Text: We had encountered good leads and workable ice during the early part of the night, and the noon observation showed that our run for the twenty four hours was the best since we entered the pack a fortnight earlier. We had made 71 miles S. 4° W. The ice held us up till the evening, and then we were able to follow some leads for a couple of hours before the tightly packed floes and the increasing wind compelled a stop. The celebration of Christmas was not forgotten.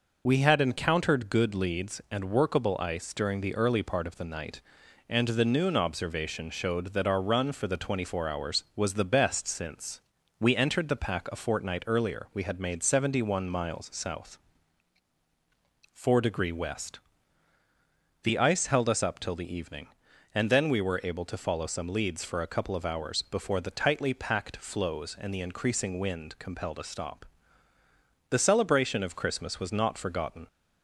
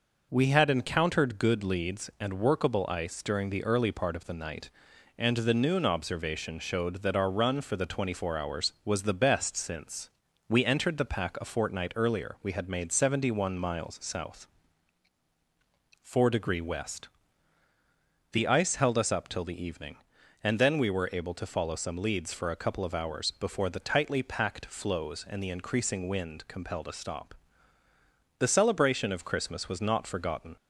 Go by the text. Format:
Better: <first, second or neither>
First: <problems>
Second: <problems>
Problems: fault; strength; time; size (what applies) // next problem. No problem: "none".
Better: second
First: loses the start of "We"; at 0.2 s; 30 ms // pauses between "since" and "we"; at 9.9 s; 0.40 s long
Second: pauses between "since" and "we"; at 10.0 s; 0.40 s long